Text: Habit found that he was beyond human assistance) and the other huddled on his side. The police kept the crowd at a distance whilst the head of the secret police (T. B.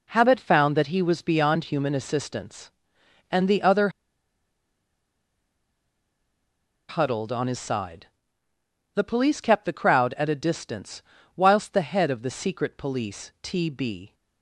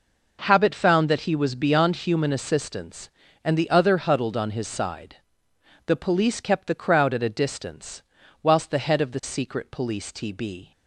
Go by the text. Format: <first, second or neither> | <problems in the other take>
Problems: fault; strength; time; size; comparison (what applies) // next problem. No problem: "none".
second | pauses between "other" and "huddled"; strong; at 3.8 s; 3.0 s long // pauses between "distance" and "whilst"; slight; at 11.0 s; 0.34 s long; also in the second